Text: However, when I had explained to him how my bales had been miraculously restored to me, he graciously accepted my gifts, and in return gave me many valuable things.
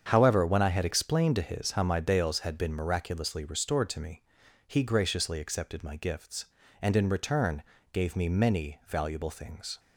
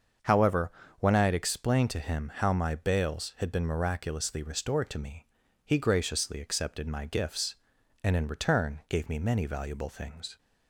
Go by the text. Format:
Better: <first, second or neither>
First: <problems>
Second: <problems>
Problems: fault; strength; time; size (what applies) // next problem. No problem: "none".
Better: second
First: starts louder than the rest; strong; until 1.0 s; 7.5 dB // says "his" for "him"; at 1.4 s // pauses between "return" and "gave"; slight; at 7.6 s; 0.30 s long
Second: starts louder than the rest; until 1.5 s; 6.5 dB